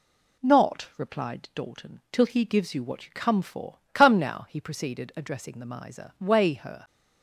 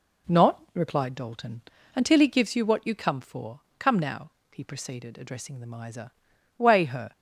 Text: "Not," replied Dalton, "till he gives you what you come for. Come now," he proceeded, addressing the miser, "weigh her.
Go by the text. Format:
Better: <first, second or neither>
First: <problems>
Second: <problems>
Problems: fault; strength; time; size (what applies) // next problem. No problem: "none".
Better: first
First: none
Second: says "until" for "till"; at 1.9 s